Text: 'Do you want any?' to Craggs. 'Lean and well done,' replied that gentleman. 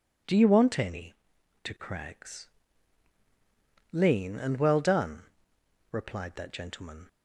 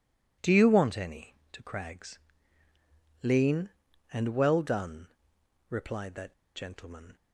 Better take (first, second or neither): first